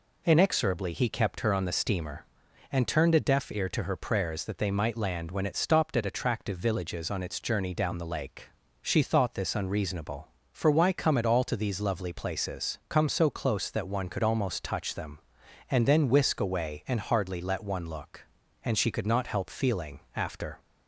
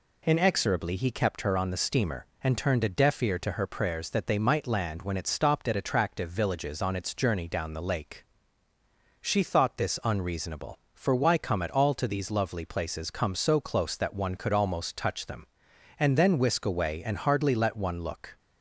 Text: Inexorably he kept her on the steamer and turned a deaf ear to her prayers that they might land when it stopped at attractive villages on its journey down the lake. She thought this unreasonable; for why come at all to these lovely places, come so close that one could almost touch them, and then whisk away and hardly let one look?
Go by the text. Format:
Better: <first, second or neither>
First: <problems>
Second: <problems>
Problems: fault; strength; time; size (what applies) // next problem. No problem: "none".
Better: second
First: goes on to say "And she could not help feeling after"; strong; from 18.6 s on; 1.9 s long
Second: none